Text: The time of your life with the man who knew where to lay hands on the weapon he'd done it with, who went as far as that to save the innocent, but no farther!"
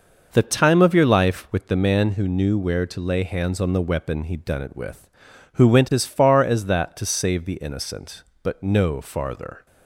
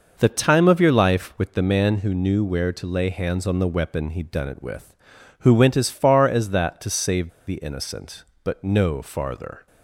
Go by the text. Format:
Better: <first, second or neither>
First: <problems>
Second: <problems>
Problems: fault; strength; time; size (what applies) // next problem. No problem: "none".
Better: first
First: none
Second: pauses between "save" and "the"; slight; at 7.2 s; 0.19 s long